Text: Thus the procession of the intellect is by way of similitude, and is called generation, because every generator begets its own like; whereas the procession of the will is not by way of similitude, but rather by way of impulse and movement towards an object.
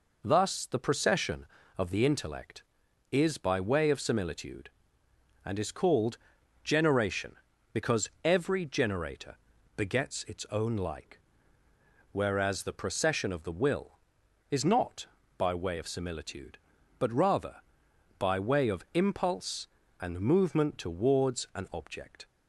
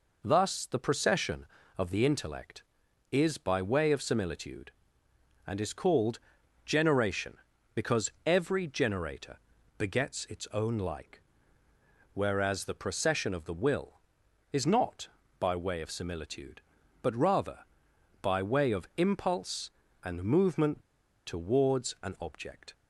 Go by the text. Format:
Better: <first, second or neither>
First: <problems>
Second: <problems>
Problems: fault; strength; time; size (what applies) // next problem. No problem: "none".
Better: first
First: pauses between "called" and "generation"; noticeable; at 6.1 s; 0.48 s long // pauses between "because" and "every"; slight; at 8.0 s; 0.16 s long // pauses between "generator" and "begets"; at 9.3 s; 0.40 s long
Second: pauses between "called" and "generation"; noticeable; at 6.1 s; 0.48 s long // pauses between "because" and "every"; slight; at 8.1 s; 0.16 s long // pauses between "generator" and "begets"; at 9.3 s; 0.40 s long // pauses between "movement" and "towards"; noticeable; at 20.8 s; 0.46 s long